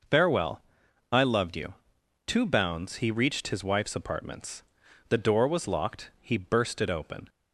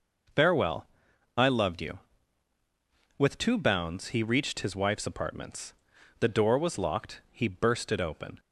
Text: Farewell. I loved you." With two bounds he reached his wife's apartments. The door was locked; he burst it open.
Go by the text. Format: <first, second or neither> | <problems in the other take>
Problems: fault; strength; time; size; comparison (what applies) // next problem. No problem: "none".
second | skips "With"; at 2.0 s